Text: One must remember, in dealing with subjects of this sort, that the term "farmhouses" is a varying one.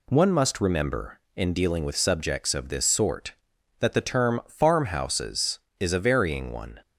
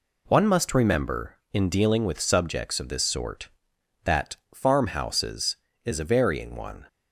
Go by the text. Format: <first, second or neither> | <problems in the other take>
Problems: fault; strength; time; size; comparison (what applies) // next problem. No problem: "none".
first | skips "the term"; at 4.4 s